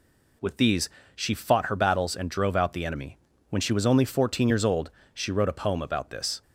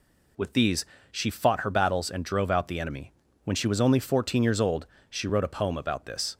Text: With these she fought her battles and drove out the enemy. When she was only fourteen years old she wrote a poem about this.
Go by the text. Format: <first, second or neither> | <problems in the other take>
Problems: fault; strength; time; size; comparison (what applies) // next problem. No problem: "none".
neither | pauses between "these" and "she"; slight; the same in both // pauses between "old" and "she"; slight; the same in both